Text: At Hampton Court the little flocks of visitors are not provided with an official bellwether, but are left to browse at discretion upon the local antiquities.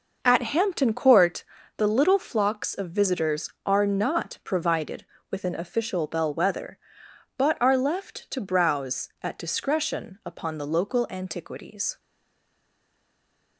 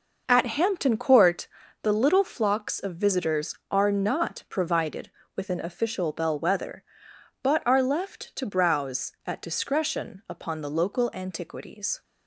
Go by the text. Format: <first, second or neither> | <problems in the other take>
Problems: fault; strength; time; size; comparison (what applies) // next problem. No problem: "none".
second | pauses between "Court" and "the"; slight; at 1.4 s; 0.34 s long; slight in the second // stays silent after the last word; noticeable; from 11.9 s on; 1.6 s long